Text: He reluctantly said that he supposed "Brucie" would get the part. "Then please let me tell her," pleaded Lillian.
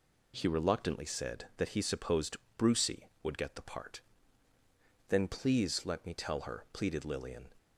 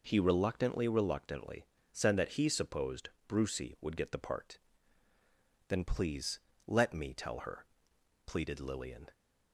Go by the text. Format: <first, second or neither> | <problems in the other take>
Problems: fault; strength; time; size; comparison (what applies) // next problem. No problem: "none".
first | says "reluctantly" twice; at 0.8 s // pauses between "supposed" and "Brucie"; slight; at 3.0 s; 0.18 s long; slight in the first // pauses between "please" and "let"; slight; at 6.3 s; 0.30 s long